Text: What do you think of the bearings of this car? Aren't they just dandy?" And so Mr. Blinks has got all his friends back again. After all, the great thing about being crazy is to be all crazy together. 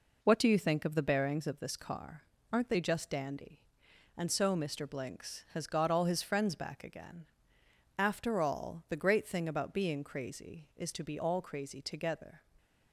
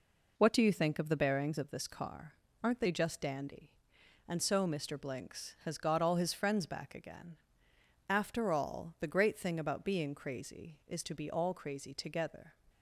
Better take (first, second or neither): neither